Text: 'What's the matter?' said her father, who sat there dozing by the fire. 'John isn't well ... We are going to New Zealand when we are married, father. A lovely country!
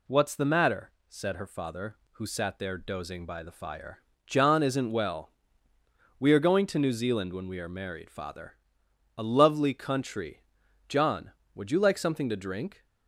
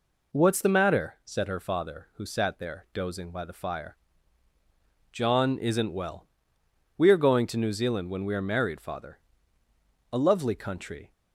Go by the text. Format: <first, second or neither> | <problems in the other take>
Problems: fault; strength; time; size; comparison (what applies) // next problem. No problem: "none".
second | goes on to say "John would you like something to drink"; strong; from 10.8 s on; 1.9 s long